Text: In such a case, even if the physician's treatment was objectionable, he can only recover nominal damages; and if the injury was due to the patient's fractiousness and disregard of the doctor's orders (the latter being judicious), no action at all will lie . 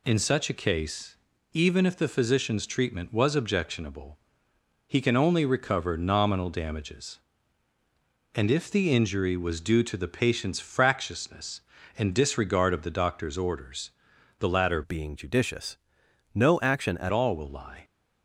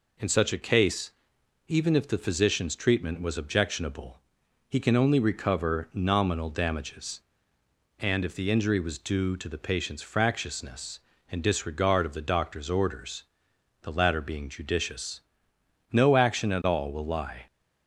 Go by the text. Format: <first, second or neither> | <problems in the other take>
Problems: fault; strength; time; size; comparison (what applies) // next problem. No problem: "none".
second | changes voice from "being" to "at"; from 14.8 to 17.1 s; 2.3 s long